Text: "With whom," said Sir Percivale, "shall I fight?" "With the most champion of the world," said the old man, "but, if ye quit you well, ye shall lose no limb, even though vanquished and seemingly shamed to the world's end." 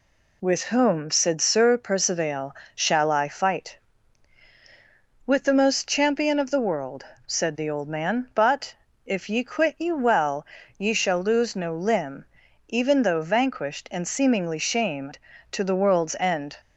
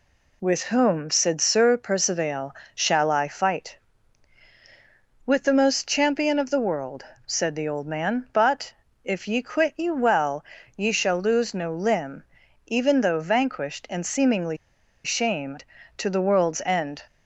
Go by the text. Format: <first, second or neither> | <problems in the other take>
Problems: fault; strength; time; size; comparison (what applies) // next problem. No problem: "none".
first | pauses between "seemingly" and "shamed"; noticeable; at 14.5 s; 0.47 s long